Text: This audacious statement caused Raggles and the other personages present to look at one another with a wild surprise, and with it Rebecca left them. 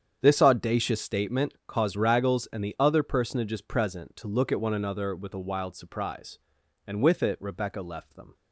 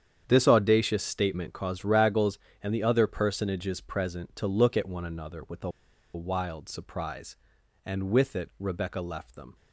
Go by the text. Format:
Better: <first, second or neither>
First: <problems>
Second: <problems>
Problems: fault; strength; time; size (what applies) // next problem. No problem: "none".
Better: first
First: starts louder than the rest; strong; until 1.2 s; 8 dB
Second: starts louder than the rest; strong; until 1.2 s; 8.5 dB // pauses between "a" and "wild"; at 5.6 s; 0.44 s long